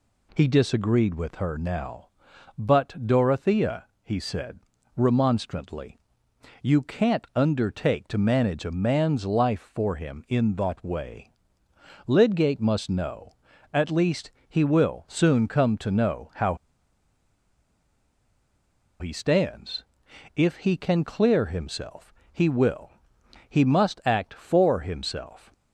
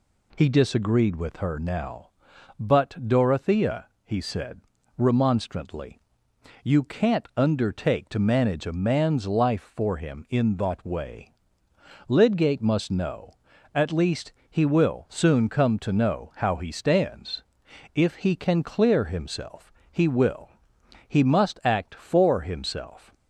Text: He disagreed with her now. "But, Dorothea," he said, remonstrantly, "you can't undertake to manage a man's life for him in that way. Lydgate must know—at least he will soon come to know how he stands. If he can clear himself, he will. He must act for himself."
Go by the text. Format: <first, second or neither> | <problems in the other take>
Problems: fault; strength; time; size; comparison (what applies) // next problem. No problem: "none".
second | pauses between "least" and "he"; slight; at 14.2 s; 0.18 s long; slight in the second // pauses between "how" and "he"; strong; at 16.5 s; 2.4 s long